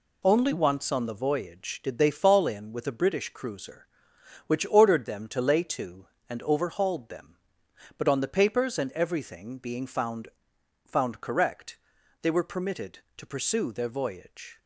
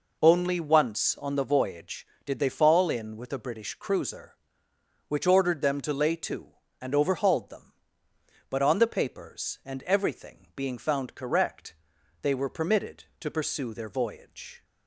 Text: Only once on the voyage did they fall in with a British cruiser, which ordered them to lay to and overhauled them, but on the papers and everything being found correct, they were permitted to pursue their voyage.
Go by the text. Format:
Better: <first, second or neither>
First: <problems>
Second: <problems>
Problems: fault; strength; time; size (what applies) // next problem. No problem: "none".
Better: second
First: says "found" twice; at 10.8 s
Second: none